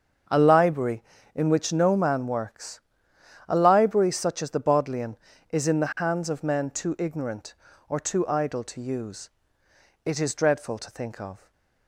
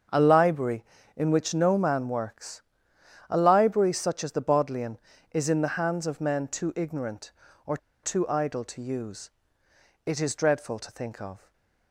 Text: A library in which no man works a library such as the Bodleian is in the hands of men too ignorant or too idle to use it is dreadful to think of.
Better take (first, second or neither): first